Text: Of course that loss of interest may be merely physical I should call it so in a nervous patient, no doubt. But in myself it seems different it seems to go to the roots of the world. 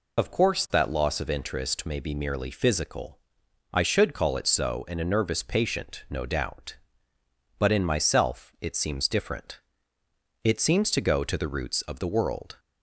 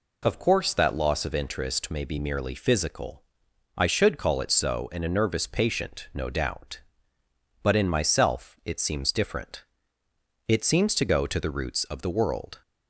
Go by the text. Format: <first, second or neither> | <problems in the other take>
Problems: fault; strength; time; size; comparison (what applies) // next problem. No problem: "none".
second | loses the start of "Of"; at 0.1 s; 30 ms // pauses between "physical" and "I"; noticeable; at 3.1 s; 0.54 s long; noticeable in the second // pauses between "different" and "it"; noticeable; at 9.6 s; 0.82 s long; noticeable in the second